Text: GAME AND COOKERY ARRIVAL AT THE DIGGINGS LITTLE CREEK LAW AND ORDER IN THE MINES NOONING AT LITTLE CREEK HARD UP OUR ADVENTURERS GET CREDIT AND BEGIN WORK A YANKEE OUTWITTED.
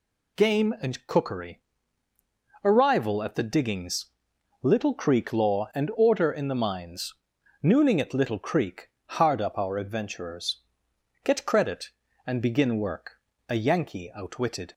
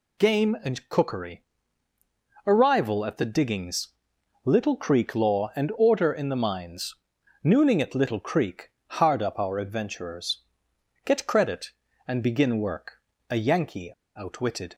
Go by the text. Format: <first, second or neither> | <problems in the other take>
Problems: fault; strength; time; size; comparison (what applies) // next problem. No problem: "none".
first | pauses between "COOKERY" and "ARRIVAL"; at 1.4 s; 1.0 s long; also in the first // pauses between "DIGGINGS" and "LITTLE"; noticeable; at 3.8 s; 0.56 s long; noticeable in the first // pauses between "MINES" and "NOONING"; noticeable; at 6.9 s; 0.48 s long; noticeable in the first // pauses between "CREEK" and "HARD"; slight; at 8.6 s; 0.16 s long; slight in the first // pauses between "ADVENTURERS" and "GET"; noticeable; at 10.4 s; 0.62 s long; noticeable in the first // pauses between "WORK" and "A"; slight; at 12.9 s; 0.30 s long; slight in the first // pauses between "YANKEE" and "OUTWITTED"; slight; at 13.9 s; 0.24 s long